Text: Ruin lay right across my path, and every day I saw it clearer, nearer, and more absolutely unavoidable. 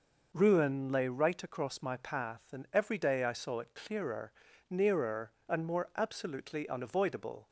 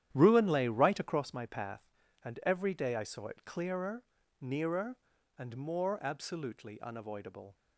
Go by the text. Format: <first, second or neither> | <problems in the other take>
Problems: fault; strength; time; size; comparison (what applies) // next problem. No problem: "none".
first | starts louder than the rest; strong; until 1.4 s; 10.5 dB